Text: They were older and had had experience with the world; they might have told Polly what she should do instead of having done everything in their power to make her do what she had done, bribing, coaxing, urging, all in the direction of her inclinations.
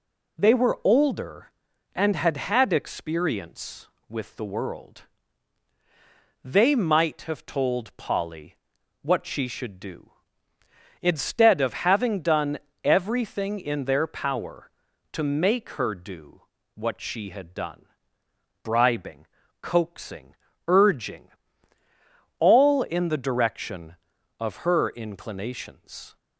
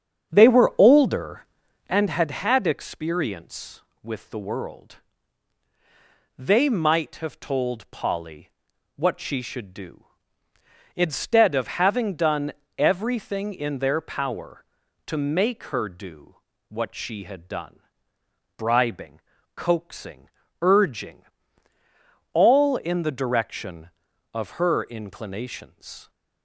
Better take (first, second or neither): first